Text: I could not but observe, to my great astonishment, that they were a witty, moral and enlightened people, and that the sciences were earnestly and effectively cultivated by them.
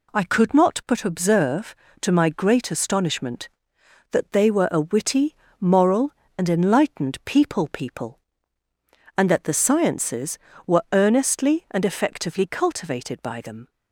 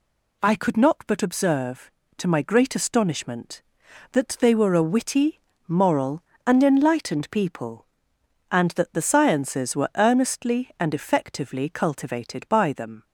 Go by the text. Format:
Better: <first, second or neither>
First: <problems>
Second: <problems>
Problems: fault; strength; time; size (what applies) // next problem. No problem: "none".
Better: second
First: says "people" twice; at 7.7 s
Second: none